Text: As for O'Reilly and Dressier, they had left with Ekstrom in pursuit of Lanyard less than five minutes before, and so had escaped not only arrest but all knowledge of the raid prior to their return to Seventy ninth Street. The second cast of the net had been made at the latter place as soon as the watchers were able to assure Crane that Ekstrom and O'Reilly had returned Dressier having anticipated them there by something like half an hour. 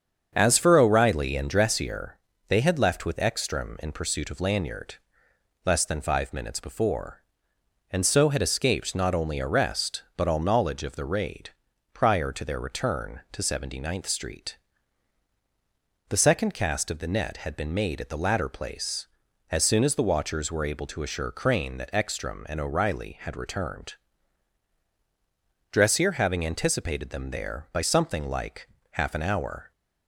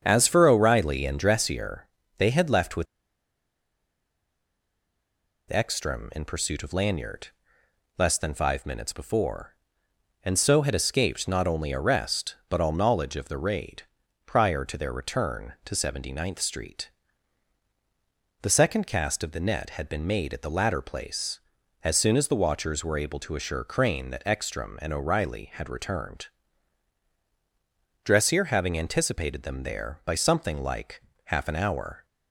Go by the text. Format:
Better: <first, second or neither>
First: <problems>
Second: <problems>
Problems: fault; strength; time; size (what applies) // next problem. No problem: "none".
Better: first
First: starts louder than the rest; strong; until 1.3 s; 7.5 dB // pauses between "Lanyard" and "less"; noticeable; at 4.9 s; 0.70 s long // pauses between "raid" and "prior"; at 11.5 s; 0.42 s long // pauses between "returned" and "Dressier"; strong; at 23.9 s; 1.7 s long // pauses between "like" and "half"; slight; at 28.6 s; 0.22 s long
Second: starts louder than the rest; strong; until 1.0 s; 7.5 dB // pauses between "with" and "Ekstrom"; strong; at 2.8 s; 2.6 s long // pauses between "Lanyard" and "less"; noticeable; at 7.2 s; 0.70 s long // pauses between "raid" and "prior"; at 13.8 s; 0.42 s long // pauses between "returned" and "Dressier"; strong; at 26.2 s; 1.7 s long // pauses between "like" and "half"; slight; at 31.0 s; 0.22 s long